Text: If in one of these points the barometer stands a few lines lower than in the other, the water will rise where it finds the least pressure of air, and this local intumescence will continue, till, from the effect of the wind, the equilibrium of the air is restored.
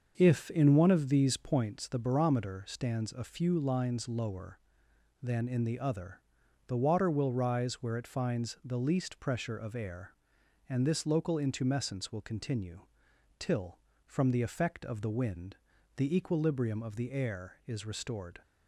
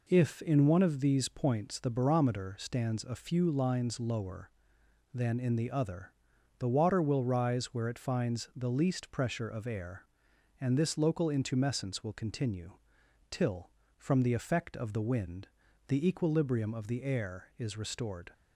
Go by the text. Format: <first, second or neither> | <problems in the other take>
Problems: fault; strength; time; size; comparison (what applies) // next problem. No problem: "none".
second | starts louder than the rest; until 1.7 s; 6.5 dB